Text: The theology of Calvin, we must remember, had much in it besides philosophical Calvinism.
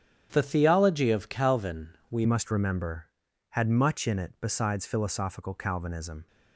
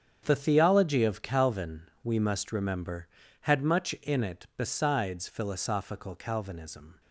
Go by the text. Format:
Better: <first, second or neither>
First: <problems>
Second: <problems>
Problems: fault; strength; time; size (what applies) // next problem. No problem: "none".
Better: second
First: starts louder than the rest; strong; until 1.3 s; 9 dB // changes voice at "must"; from 2.2 s on; 4.0 s long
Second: starts louder than the rest; strong; until 1.2 s; 8 dB